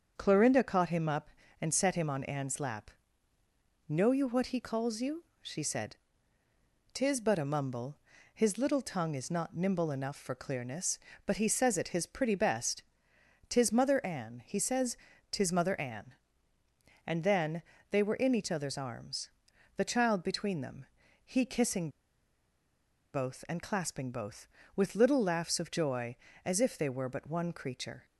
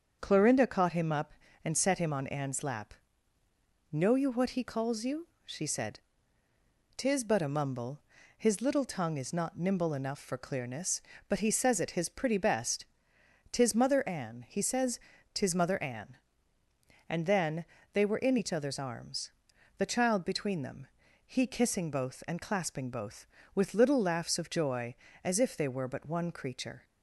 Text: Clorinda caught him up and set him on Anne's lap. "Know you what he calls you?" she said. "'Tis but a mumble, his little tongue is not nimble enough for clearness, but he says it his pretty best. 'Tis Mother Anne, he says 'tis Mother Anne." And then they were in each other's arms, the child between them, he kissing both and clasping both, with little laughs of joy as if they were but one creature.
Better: second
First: starts louder than the rest; until 1.1 s; 7 dB // pauses between "says" and "tis"; slight; at 14.9 s; 0.34 s long // pauses between "then" and "they"; slight; at 17.6 s; 0.28 s long // pauses between "kissing" and "both"; strong; at 21.8 s; 1.2 s long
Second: starts louder than the rest; until 1.2 s; 7 dB // pauses between "says" and "tis"; slight; at 14.9 s; 0.34 s long // pauses between "then" and "they"; slight; at 17.6 s; 0.28 s long

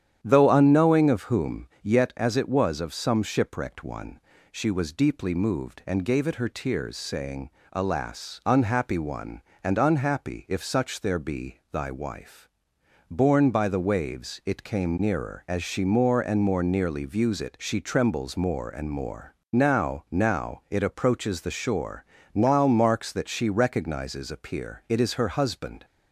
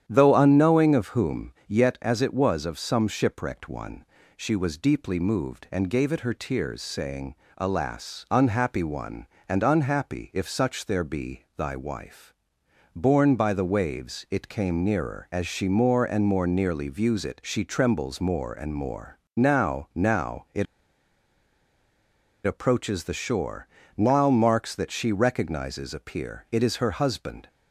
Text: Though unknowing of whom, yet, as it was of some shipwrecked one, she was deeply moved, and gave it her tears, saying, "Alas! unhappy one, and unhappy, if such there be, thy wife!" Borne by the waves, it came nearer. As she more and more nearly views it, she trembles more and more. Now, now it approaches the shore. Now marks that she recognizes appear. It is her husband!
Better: first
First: starts louder than the rest; strong; until 1.2 s; 9.5 dB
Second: starts louder than the rest; strong; until 1.0 s; 9.5 dB // pauses between "it" and "approaches"; strong; at 20.6 s; 1.8 s long

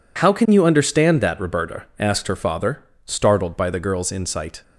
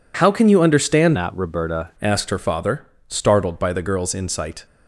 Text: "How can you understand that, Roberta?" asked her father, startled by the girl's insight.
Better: first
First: none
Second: changes voice from "that" to "Roberta"; from 1.1 to 1.8 s; 0.7 s long

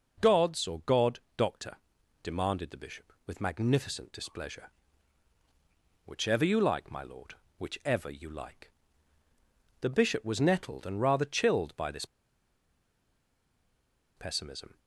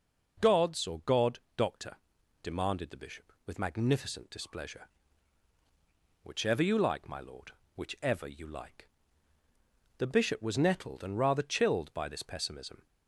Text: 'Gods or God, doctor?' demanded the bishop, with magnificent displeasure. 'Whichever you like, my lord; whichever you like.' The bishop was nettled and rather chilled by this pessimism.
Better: second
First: pauses between "this" and "pessimism"; strong; at 12.0 s; 2.1 s long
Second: none

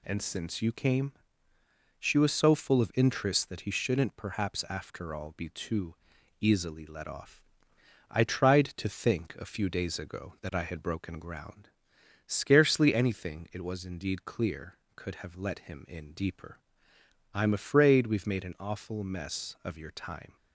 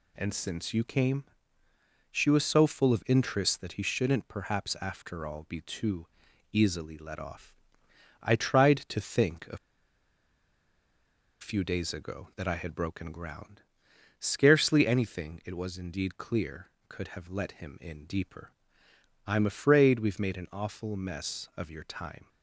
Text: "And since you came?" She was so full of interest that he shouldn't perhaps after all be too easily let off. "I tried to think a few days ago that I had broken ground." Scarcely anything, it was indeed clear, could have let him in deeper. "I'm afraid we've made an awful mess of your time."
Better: first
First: pauses between "too" and "easily"; noticeable; at 5.9 s; 0.46 s long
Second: pauses between "too" and "easily"; noticeable; at 6.0 s; 0.46 s long // pauses between "a" and "few"; strong; at 9.5 s; 1.8 s long

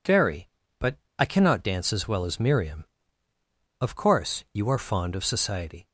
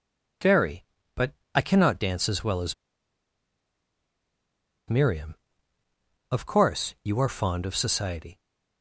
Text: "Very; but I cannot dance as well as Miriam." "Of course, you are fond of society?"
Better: first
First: pauses between "but" and "I"; slight; at 0.9 s; 0.22 s long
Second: pauses between "but" and "I"; slight; at 1.3 s; 0.22 s long // pauses between "as" and "Miriam"; strong; at 2.7 s; 2.1 s long

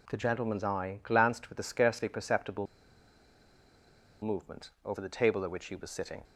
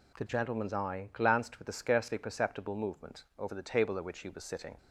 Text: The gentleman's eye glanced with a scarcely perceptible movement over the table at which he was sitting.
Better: second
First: pauses between "perceptible" and "movement"; strong; at 2.6 s; 1.5 s long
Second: none

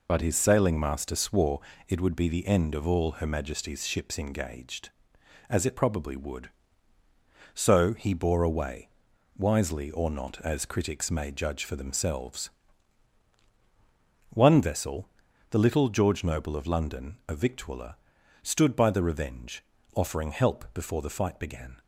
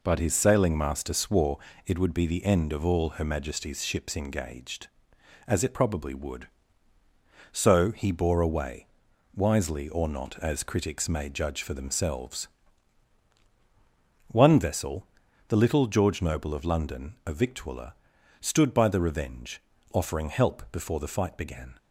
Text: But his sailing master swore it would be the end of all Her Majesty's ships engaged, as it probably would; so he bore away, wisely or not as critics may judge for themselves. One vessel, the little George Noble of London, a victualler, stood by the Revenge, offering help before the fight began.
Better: second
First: loses the start of "But"; at 0.0 s; 55 ms // pauses between "swore" and "it"; slight; at 1.6 s; 0.26 s long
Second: pauses between "swore" and "it"; slight; at 1.5 s; 0.26 s long

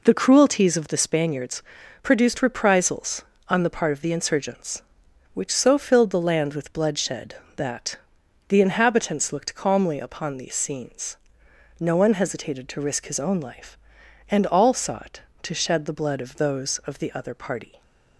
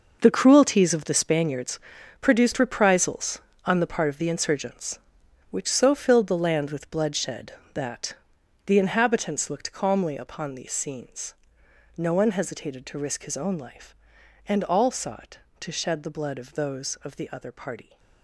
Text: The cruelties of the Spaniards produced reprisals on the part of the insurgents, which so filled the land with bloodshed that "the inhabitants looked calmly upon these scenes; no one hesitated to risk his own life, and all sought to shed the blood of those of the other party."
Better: first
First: pauses between "Spaniards" and "produced"; at 1.6 s; 0.38 s long // pauses between "that" and "the"; noticeable; at 7.9 s; 0.50 s long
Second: gets quieter; strong; throughout; 12.5 dB // pauses between "Spaniards" and "produced"; at 1.7 s; 0.40 s long // pauses between "that" and "the"; noticeable; at 8.1 s; 0.50 s long

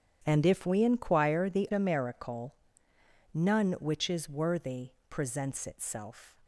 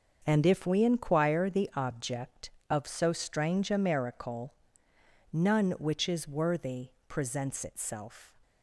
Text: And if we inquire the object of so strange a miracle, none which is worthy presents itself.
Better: second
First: starts louder than the rest; strong; until 1.2 s; 9.5 dB // skips "object of so strange"; at 1.7 s // pauses between "worthy" and "presents"; slight; at 4.8 s; 0.20 s long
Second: starts louder than the rest; until 1.2 s; 6.5 dB // pauses between "worthy" and "presents"; slight; at 6.8 s; 0.20 s long

